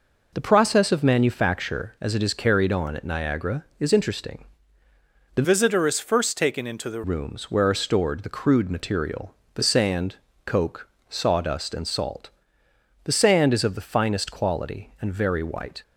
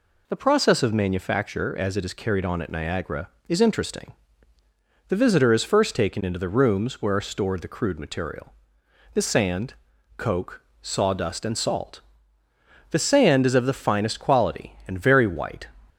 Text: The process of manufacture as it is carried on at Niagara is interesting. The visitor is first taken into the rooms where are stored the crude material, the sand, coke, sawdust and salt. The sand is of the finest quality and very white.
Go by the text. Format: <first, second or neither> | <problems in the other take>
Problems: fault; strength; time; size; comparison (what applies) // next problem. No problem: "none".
second | changes voice from "visitor" to "the"; from 5.4 to 7.0 s; 1.6 s long